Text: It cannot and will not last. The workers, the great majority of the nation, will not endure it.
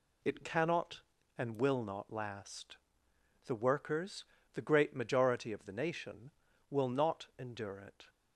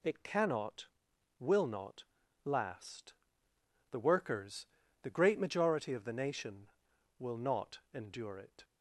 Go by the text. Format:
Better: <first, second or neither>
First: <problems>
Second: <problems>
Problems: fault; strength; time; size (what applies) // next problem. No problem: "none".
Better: first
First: none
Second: skips "and"; at 1.1 s // pauses between "not" and "last"; at 2.0 s; 0.42 s long // pauses between "not" and "endure"; slight; at 7.7 s; 0.16 s long